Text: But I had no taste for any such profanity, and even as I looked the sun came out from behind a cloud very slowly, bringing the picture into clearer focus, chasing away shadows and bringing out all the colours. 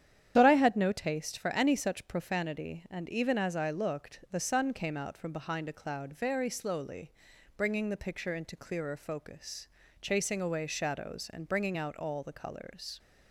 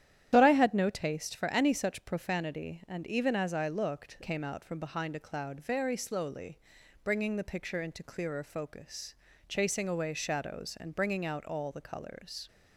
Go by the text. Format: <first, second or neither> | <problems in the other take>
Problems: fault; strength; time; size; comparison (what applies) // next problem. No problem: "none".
first | starts louder than the rest; strong; until 1.3 s; 11 dB; strong in the first // skips "the sun"; at 4.1 s